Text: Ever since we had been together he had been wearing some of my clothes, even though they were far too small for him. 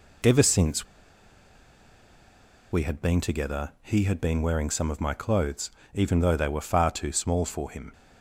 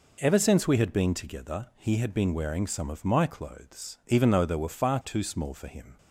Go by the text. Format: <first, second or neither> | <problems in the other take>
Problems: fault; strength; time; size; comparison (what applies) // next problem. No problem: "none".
second | pauses between "since" and "we"; strong; at 0.8 s; 1.8 s long